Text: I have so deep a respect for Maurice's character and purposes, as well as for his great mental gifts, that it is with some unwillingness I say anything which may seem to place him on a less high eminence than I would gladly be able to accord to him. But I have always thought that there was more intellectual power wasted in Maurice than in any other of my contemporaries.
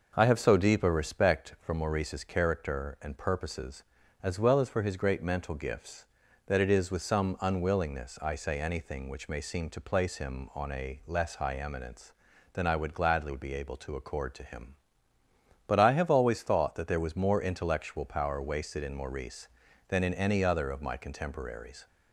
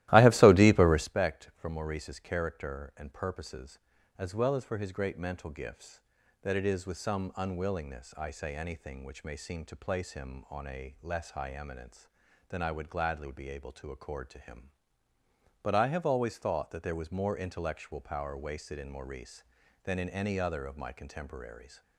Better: first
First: none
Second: starts louder than the rest; strong; until 1.2 s; 15.5 dB

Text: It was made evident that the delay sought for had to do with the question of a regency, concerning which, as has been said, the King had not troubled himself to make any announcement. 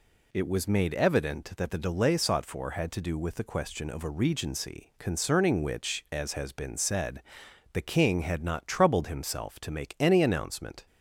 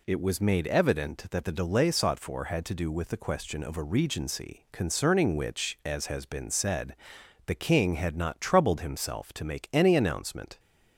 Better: neither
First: none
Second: none

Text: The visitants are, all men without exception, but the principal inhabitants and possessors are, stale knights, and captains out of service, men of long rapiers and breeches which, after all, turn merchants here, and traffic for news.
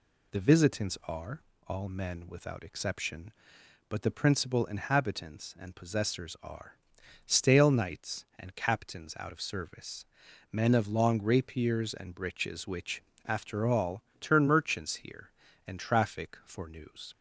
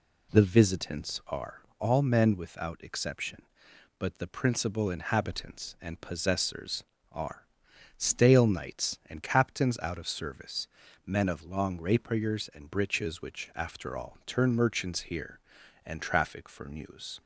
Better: neither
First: none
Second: none

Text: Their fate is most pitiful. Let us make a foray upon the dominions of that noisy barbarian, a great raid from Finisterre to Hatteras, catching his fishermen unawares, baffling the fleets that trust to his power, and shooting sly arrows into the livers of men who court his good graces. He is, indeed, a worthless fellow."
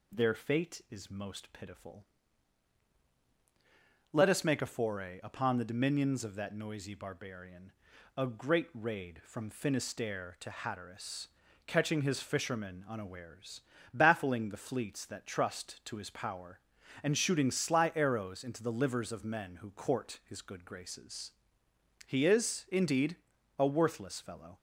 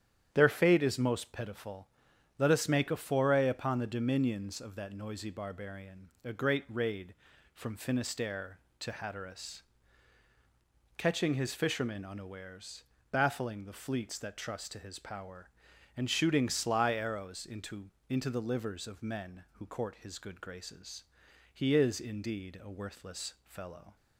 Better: first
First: none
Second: starts louder than the rest; strong; until 1.3 s; 10 dB // says "into" twice; at 18.0 s

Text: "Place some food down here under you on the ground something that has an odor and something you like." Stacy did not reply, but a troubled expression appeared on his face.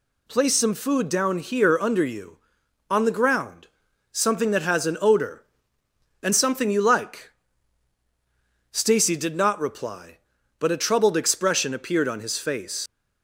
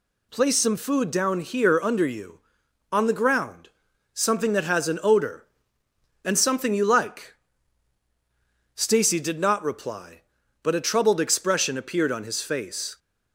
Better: second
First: pauses between "ground" and "something"; noticeable; at 3.6 s; 0.46 s long // leaves "face" unfinished; at 12.8 s; 85 ms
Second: pauses between "ground" and "something"; noticeable; at 3.6 s; 0.46 s long

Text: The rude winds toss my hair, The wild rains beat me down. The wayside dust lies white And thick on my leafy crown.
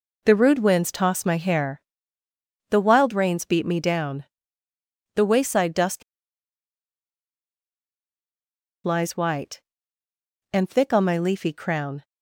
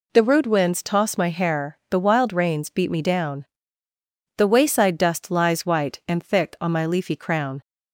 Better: second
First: pauses between "dust" and "lies"; strong; at 6.0 s; 2.8 s long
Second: none

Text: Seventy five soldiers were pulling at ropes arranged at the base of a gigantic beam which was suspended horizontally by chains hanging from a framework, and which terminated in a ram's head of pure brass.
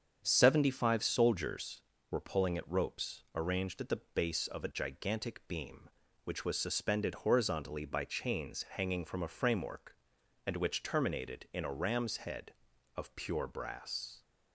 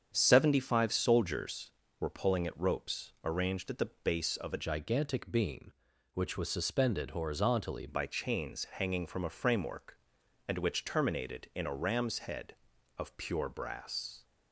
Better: first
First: starts louder than the rest; strong; until 1.2 s; 7.5 dB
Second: starts louder than the rest; strong; until 1.1 s; 8 dB // changes voice from "gigantic" to "horizontally"; from 4.6 to 7.8 s; 3.2 s long

